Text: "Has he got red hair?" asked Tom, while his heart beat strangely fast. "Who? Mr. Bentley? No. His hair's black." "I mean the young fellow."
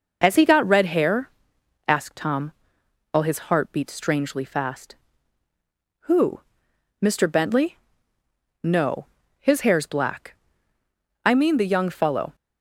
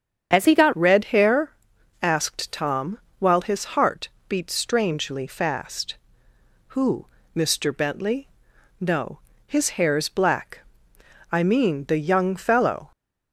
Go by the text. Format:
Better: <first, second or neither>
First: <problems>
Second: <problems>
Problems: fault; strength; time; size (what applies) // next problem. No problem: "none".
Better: first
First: none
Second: starts louder than the rest; strong; until 1.3 s; 8 dB // changes voice at "red"; from 0.7 s on; 12.2 s long // pauses between "heart" and "beat"; slight; at 4.0 s; 0.22 s long